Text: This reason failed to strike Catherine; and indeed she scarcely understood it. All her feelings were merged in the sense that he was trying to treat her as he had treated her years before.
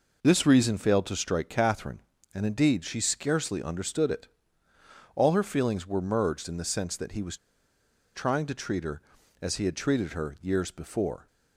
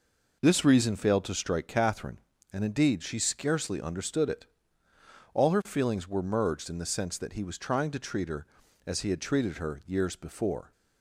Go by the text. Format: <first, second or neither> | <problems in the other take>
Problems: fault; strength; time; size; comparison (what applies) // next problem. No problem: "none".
second | pauses between "was" and "trying"; noticeable; at 7.3 s; 0.76 s long